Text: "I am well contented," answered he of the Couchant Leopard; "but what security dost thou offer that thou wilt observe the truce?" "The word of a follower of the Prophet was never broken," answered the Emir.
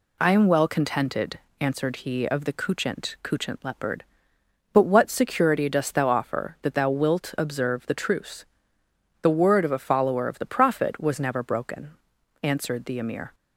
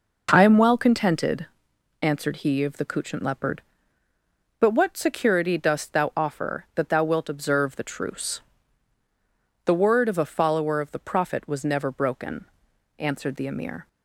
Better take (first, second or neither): second